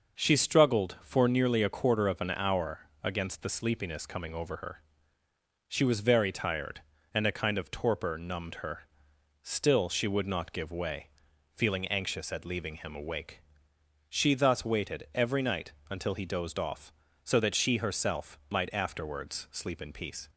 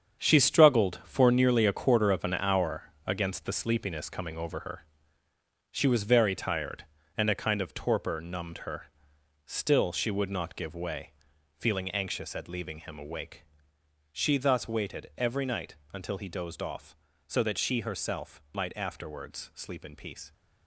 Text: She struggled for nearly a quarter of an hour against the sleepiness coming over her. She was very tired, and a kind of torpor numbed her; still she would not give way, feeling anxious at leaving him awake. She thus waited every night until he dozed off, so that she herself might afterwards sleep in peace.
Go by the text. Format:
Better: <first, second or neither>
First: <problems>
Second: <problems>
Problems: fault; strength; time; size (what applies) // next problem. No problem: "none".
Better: first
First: starts louder than the rest; noticeable; until 1.2 s; 6 dB // pauses between "hour" and "against"; slight; at 2.8 s; 0.16 s long // pauses between "night" and "until"; slight; at 15.7 s; 0.16 s long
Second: gets quieter; strong; throughout; 10.5 dB // starts louder than the rest; strong; until 1.2 s; 8 dB // pauses between "hour" and "against"; slight; at 2.9 s; 0.16 s long // pauses between "night" and "until"; slight; at 15.7 s; 0.16 s long